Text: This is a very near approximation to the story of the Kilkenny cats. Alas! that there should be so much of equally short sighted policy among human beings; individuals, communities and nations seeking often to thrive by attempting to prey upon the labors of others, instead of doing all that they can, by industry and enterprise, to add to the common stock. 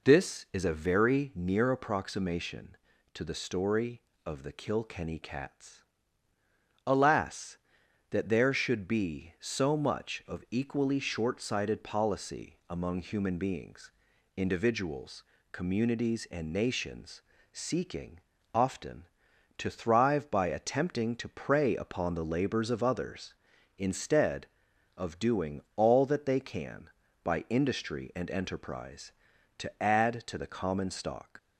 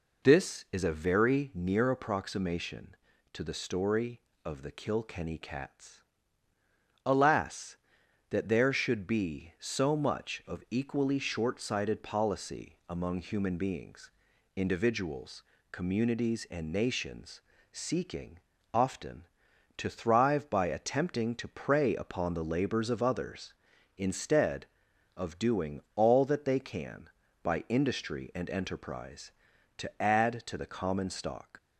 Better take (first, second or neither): neither